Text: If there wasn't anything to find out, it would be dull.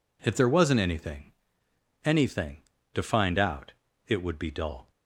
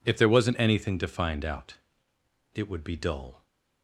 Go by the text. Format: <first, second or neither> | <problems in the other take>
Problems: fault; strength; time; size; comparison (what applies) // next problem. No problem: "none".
second | says "anything" twice; at 2.0 s